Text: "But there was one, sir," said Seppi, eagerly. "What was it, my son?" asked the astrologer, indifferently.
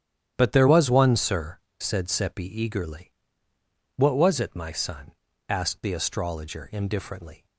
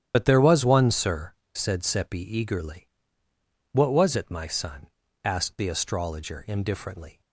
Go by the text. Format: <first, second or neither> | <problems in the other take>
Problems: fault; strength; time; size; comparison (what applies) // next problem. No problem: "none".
first | loses the start of "But"; at 0.1 s; 55 ms // starts louder than the rest; strong; until 1.1 s; 10.5 dB; strong in the first